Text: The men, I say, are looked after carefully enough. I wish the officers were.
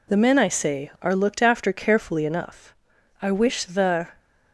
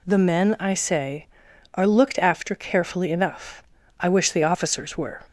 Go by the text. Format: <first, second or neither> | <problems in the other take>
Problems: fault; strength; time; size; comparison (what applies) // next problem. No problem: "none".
second | stops before "officers were"; at 4.1 s